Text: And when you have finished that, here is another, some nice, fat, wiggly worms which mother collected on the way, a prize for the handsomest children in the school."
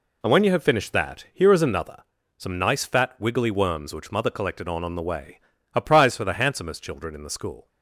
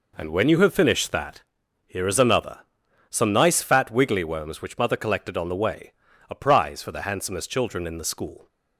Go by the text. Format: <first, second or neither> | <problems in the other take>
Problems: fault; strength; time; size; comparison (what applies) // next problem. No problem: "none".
second | says "on" twice; at 4.8 s